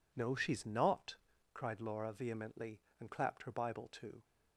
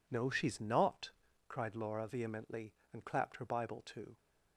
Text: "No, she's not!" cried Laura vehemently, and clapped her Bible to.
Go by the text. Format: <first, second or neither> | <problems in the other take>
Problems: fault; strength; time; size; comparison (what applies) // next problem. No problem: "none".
neither | none